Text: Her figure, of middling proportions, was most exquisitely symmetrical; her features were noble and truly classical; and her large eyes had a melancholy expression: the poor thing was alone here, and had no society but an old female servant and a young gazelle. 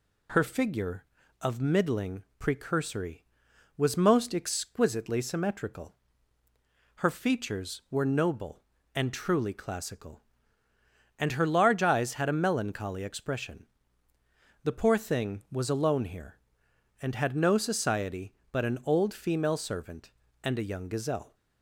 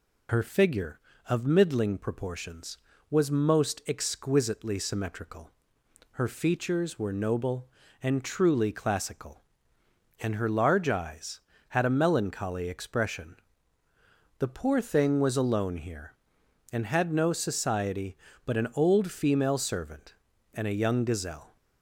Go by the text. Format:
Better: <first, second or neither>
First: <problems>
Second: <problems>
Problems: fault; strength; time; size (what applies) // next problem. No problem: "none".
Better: second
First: says "precursory" for "proportions"; at 2.3 s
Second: none